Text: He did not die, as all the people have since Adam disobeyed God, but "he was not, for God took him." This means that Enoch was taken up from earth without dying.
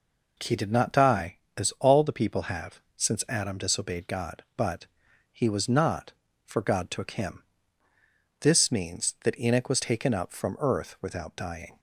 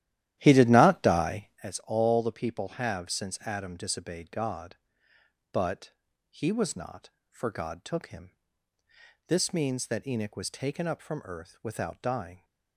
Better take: first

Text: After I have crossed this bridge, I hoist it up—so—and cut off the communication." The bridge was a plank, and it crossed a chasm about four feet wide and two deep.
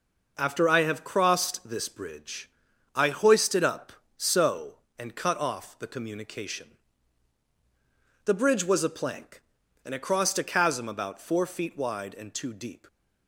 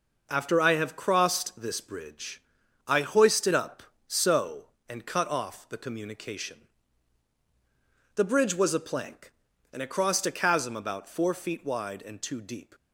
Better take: neither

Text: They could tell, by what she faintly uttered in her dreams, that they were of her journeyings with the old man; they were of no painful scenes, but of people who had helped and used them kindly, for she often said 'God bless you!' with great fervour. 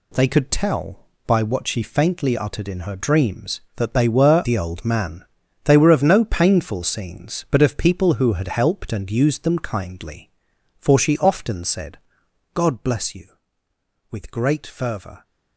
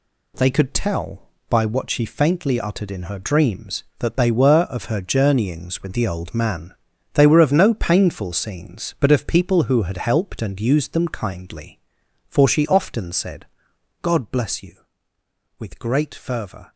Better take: second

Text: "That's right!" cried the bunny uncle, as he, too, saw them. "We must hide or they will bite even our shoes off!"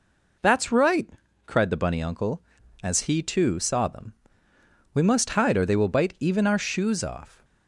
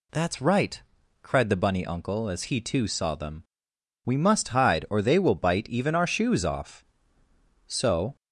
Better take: first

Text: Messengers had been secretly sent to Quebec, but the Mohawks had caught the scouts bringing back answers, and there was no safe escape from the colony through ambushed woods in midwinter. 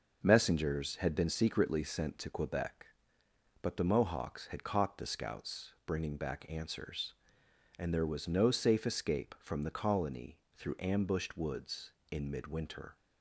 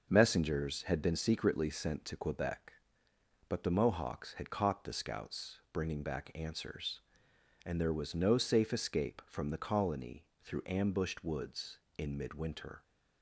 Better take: neither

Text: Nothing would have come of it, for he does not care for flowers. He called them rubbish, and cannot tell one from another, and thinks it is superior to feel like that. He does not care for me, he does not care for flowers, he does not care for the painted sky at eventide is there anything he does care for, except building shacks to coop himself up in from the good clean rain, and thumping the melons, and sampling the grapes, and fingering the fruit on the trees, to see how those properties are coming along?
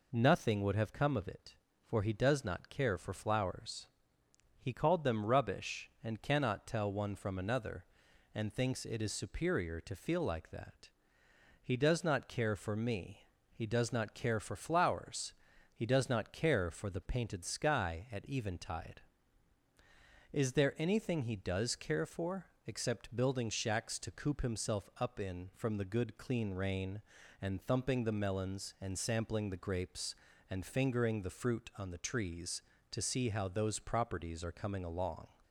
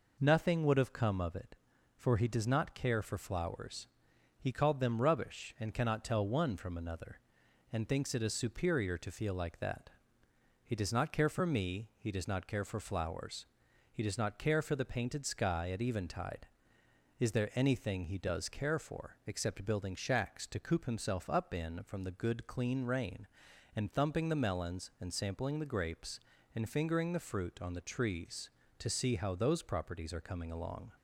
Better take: neither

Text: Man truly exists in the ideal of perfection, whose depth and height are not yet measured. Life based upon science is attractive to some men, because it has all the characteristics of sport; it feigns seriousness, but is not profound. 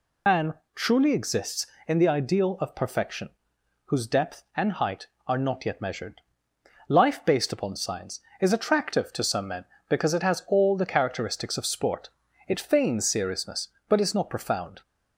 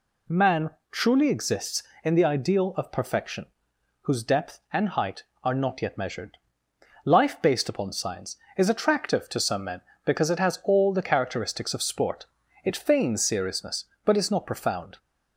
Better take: second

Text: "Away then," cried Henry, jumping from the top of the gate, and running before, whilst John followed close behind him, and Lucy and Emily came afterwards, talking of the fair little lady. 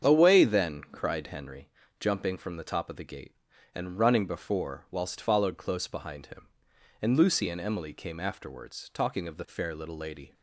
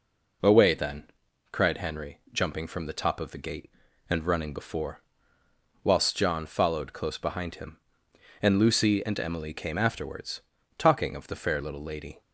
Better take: second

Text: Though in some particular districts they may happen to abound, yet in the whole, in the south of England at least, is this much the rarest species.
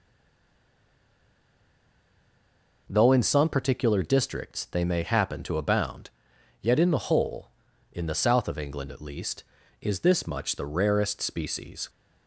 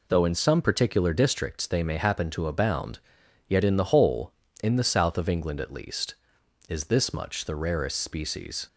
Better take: second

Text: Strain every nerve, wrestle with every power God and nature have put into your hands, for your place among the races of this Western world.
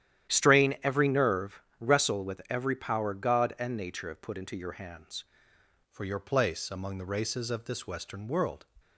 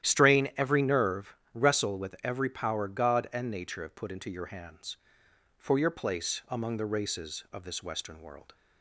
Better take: second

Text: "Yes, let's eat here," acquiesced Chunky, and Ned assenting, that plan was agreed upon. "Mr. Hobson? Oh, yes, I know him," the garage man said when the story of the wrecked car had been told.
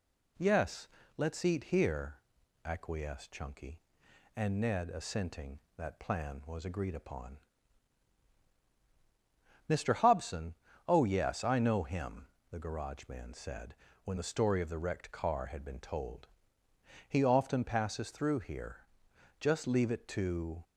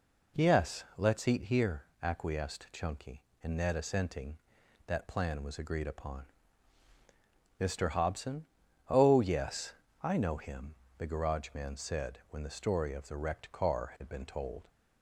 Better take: second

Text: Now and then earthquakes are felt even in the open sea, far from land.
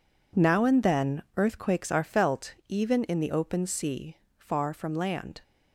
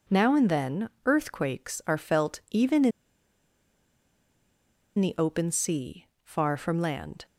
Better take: first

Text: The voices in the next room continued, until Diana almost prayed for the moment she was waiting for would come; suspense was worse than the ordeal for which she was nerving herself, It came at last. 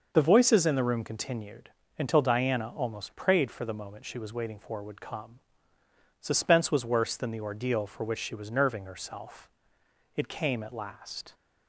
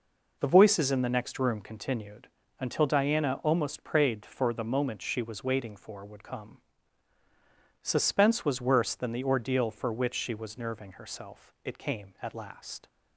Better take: second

